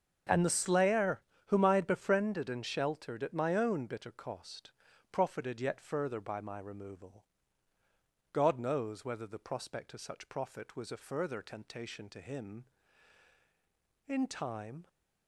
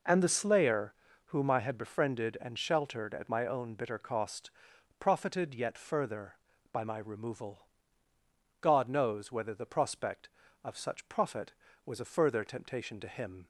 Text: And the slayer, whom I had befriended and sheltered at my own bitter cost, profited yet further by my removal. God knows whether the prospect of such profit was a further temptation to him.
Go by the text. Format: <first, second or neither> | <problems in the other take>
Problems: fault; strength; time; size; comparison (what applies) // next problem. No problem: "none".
second | starts louder than the rest; until 1.5 s; 6.5 dB // goes on to say "In time"; noticeable; from 14.0 s on; 0.82 s long